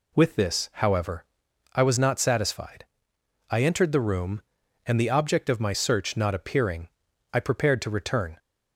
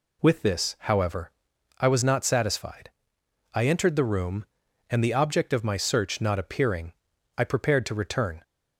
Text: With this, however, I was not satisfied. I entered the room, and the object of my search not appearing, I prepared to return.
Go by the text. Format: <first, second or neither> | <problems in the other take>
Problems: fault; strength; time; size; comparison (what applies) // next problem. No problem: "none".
neither | none